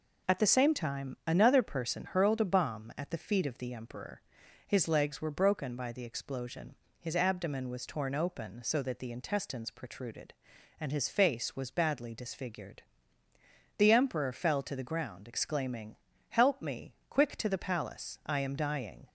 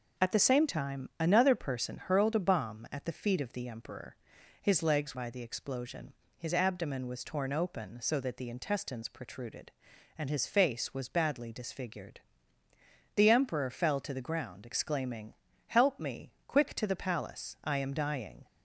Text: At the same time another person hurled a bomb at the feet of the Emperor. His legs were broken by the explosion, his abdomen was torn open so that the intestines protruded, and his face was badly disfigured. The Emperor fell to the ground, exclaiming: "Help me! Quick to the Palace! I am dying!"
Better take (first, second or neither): first